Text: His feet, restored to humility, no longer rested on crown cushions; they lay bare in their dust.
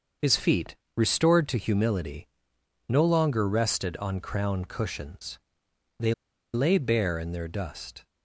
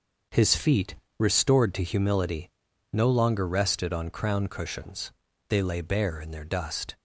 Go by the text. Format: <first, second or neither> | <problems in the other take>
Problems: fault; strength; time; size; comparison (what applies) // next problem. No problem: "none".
second | starts louder than the rest; until 1.4 s; 6.5 dB; also in the second // pauses between "they" and "lay"; at 6.1 s; 0.39 s long